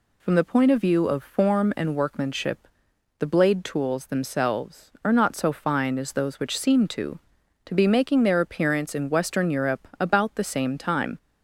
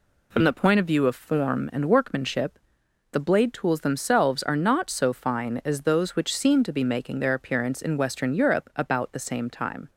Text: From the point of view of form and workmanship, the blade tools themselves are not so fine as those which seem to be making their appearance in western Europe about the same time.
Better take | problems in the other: second | says "to" twice; at 7.6 s

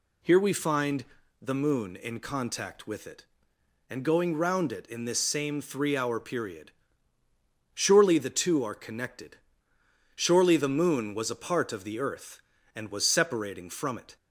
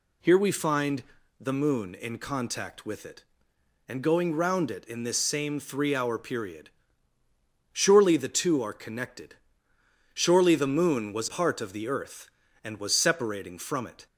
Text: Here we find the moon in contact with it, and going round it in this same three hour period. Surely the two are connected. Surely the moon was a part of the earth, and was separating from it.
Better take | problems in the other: first | pauses between "find" and "the"; at 1.0 s; 0.38 s long; also in the first // skips "a"; at 11.2 s

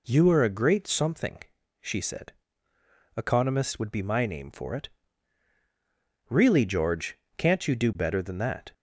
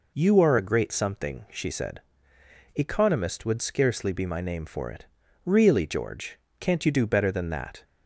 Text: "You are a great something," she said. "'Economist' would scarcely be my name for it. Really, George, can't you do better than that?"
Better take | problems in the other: second | skips "scarcely"; at 3.9 s

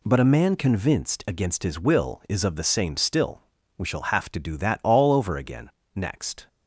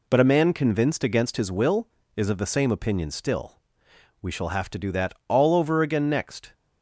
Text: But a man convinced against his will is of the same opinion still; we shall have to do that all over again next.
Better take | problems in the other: second | skips "opinion"; at 2.9 s // pauses between "again" and "next"; slight; at 5.6 s; 0.24 s long

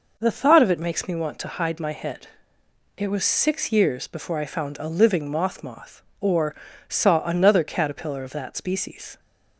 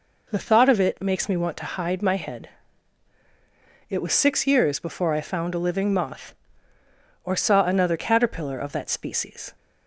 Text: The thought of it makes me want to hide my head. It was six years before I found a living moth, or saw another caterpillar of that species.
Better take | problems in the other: second | says "moth" twice; at 5.6 s // pauses between "or" and "saw"; slight; at 6.5 s; 0.34 s long

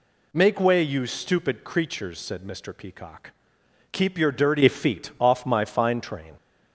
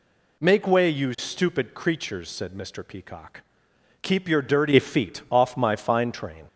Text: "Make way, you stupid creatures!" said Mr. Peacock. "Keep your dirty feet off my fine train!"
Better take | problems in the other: neither | none

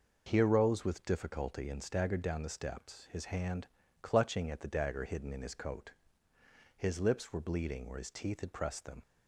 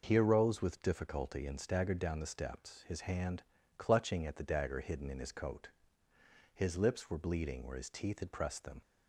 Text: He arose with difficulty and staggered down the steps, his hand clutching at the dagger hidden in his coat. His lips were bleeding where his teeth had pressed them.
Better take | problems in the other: neither | pauses between "hand" and "clutching"; slight; the same in both

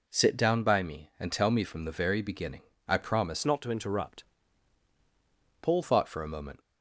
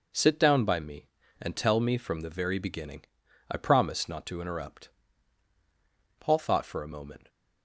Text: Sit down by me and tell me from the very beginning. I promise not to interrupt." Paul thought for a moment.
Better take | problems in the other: second | changes voice from "not" to "Paul"; from 3.4 to 5.8 s; 2.4 s long

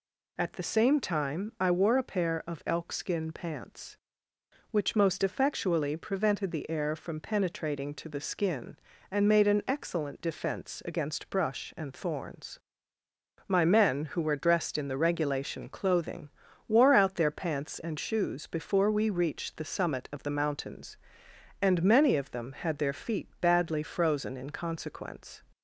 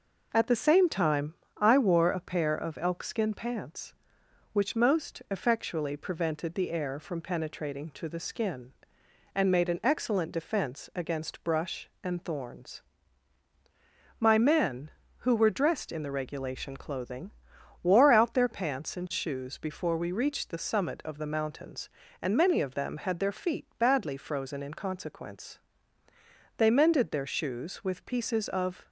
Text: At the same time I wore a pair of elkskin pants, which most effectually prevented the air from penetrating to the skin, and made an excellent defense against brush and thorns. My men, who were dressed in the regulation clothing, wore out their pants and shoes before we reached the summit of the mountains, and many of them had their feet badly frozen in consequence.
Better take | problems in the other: first | pauses between "time" and "I"; slight; at 1.3 s; 0.24 s long // goes on to say "They mended their shoes with pieces of"; strong; from 26.5 s on; 2.3 s long

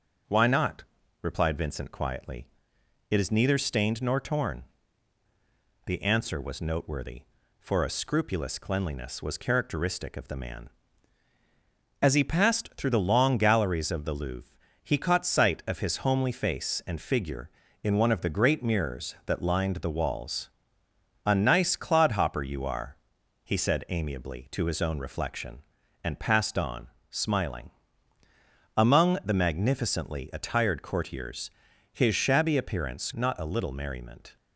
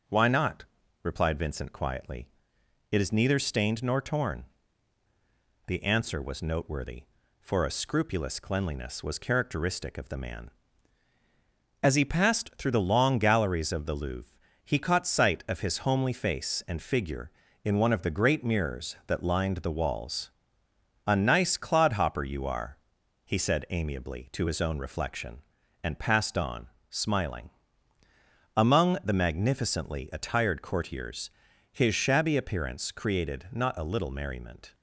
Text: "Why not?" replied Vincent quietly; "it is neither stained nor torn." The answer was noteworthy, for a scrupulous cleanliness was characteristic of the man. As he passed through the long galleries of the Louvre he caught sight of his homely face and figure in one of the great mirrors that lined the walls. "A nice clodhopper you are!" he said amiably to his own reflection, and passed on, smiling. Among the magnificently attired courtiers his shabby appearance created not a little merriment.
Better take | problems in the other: second | pauses between "Louvre" and "he"; slight; at 14.5 s; 0.26 s long; slight in the second // pauses between "courtiers" and "his"; at 31.4 s; 0.44 s long; also in the second // skips "created"; at 33.1 s

